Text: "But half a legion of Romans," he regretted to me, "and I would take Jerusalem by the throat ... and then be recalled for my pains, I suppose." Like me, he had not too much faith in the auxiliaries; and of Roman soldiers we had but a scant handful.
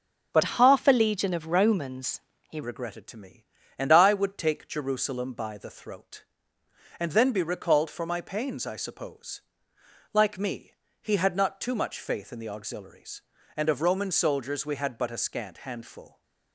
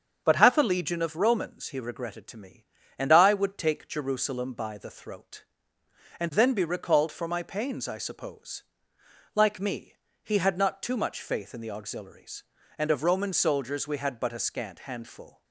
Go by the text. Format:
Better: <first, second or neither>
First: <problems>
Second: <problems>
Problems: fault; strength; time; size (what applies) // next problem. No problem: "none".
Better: second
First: starts louder than the rest; until 1.3 s; 6.5 dB // changes voice from "half" to "he"; from 0.4 to 2.6 s; 2.2 s long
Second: starts louder than the rest; strong; until 1.2 s; 7 dB